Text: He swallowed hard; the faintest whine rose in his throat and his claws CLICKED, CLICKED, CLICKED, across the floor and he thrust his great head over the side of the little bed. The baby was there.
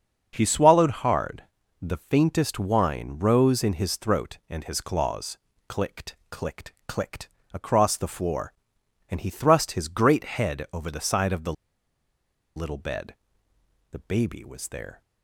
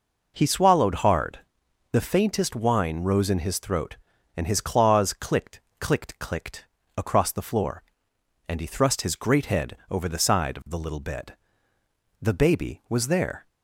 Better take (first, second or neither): second